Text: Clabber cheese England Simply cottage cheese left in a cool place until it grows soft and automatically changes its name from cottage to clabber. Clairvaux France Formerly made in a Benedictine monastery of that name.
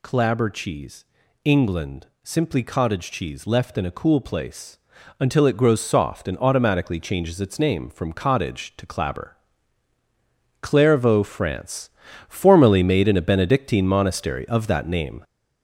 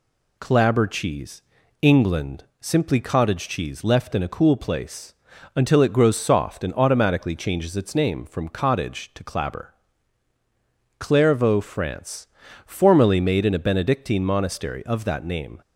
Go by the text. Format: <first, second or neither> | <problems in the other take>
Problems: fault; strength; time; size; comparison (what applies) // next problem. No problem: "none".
second | gets louder; noticeable; throughout; 5.5 dB // pauses between "cheese" and "England"; at 1.0 s; 0.38 s long; also in the second // pauses between "England" and "Simply"; slight; at 2.0 s; 0.16 s long; slight in the second // pauses between "place" and "until"; at 4.7 s; 0.42 s long; also in the second // pauses between "France" and "Formerly"; at 11.8 s; 0.38 s long; also in the second